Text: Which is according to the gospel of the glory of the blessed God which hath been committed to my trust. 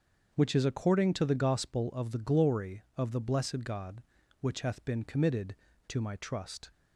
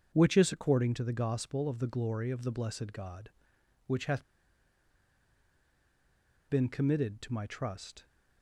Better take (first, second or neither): first